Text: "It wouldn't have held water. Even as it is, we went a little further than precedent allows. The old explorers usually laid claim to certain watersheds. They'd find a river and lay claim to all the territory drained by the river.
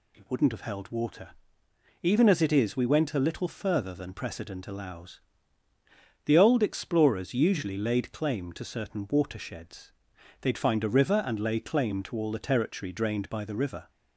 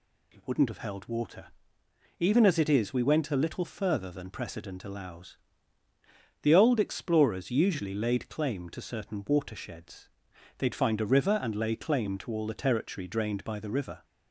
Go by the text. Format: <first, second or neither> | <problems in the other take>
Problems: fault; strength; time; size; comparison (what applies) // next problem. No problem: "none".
neither | none